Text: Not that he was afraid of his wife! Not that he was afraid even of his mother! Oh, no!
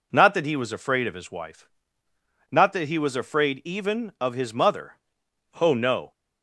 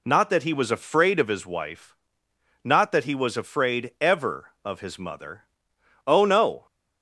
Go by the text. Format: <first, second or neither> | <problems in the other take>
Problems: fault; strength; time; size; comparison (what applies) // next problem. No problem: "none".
first | says "ever" for "even"; at 3.9 s